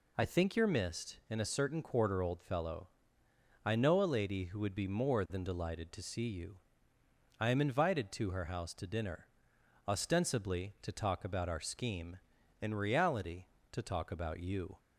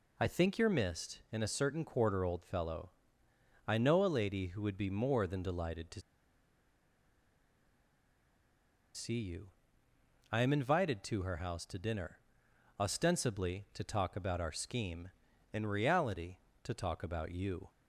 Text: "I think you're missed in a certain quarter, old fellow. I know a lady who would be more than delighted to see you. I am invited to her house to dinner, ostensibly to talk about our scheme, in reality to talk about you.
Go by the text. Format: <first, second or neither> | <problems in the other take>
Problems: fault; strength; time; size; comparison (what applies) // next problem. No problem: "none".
first | pauses between "to" and "see"; strong; at 6.0 s; 2.9 s long